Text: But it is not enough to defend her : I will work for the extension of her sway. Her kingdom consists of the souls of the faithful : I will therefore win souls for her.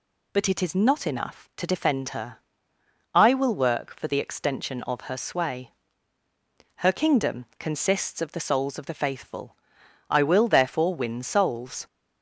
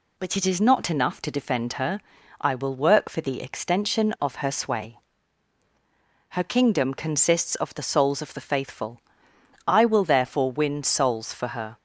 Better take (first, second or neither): second